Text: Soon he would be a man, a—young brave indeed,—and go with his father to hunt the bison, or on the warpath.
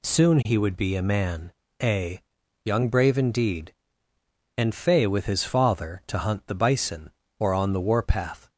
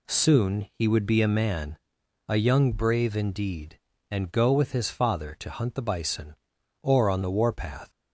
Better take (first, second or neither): second